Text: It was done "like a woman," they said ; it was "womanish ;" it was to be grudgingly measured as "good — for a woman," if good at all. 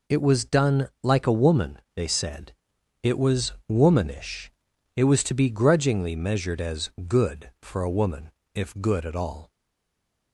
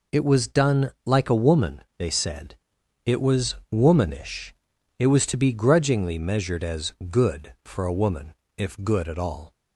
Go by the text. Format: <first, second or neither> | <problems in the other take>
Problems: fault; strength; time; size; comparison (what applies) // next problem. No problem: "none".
second | pauses between "done" and "like"; slight; at 0.8 s; 0.16 s long; slight in the second // pauses between "was" and "womanish"; slight; at 3.5 s; 0.16 s long; slight in the second // pauses between "as" and "good"; slight; at 6.9 s; 0.18 s long; slight in the second // stays silent after the last word; slight; from 9.5 s on; 0.8 s long